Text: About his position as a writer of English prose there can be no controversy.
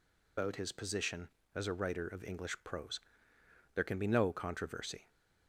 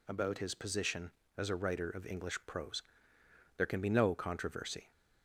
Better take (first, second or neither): second